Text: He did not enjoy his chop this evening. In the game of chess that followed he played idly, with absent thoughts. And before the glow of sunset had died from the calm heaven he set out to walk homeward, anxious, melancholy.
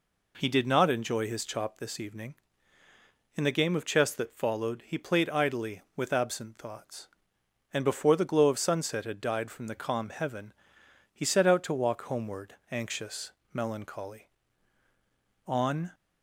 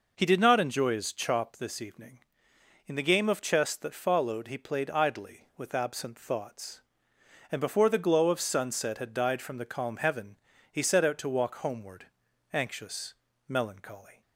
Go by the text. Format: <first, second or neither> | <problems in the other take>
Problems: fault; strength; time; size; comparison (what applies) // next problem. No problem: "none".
second | pauses between "heaven" and "he"; noticeable; at 10.5 s; 0.60 s long; slight in the second // goes on to say "On"; slight; from 15.4 s on; 0.44 s long